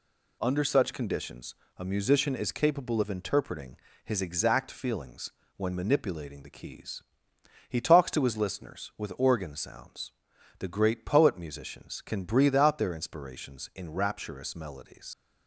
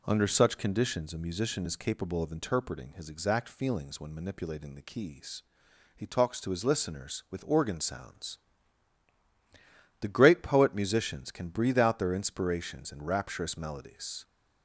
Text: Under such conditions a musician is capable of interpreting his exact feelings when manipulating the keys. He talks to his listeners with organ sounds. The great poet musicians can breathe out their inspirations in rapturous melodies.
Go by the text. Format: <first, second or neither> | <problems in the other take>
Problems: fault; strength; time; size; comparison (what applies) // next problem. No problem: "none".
second | pauses between "conditions" and "a"; slight; at 1.5 s; 0.22 s long // pauses between "interpreting" and "his"; slight; at 3.7 s; 0.26 s long // pauses between "feelings" and "when"; slight; at 5.3 s; 0.26 s long // leaves "melodies" unfinished; at 15.1 s; 95 ms